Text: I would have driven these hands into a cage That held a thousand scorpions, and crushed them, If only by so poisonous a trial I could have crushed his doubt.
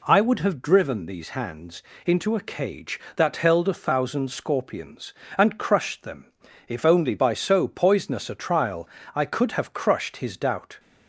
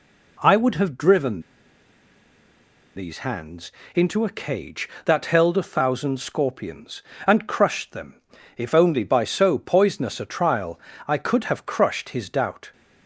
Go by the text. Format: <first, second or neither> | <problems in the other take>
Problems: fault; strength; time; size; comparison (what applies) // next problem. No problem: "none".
first | pauses between "driven" and "these"; strong; at 1.4 s; 1.5 s long // pauses between "hands" and "into"; slight; at 3.6 s; 0.24 s long; slight in the first // pauses between "trial" and "I"; slight; at 10.7 s; 0.26 s long; slight in the first